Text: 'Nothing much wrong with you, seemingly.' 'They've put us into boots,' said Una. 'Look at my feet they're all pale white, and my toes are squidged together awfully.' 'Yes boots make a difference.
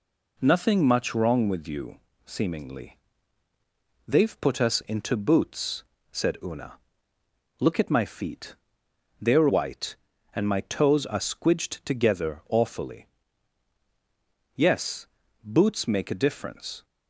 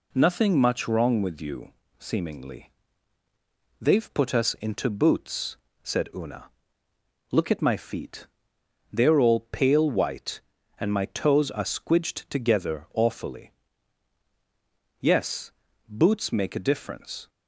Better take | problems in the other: second | pauses between "feet" and "they're"; noticeable; at 8.5 s; 0.64 s long; noticeable in the second // skips "all pale"; at 9.4 s // pauses between "Yes" and "boots"; slight; at 15.0 s; 0.36 s long; slight in the second

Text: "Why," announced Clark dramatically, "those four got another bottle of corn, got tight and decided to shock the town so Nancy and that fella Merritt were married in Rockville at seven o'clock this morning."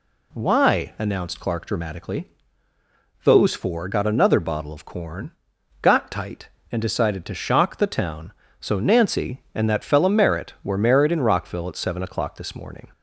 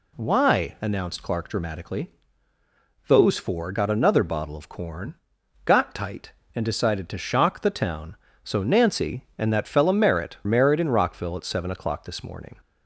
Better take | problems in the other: first | skips "were"; at 10.4 s

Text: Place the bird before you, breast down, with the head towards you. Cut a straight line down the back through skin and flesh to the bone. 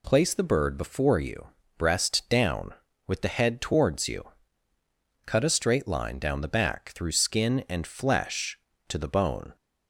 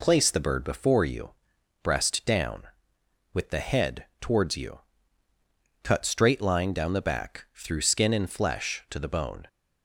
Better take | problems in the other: first | skips "a"; at 6.0 s

